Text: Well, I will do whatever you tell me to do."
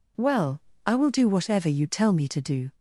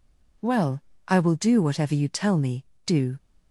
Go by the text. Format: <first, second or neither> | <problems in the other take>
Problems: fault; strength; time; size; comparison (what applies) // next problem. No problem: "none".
first | skips "to"; at 2.7 s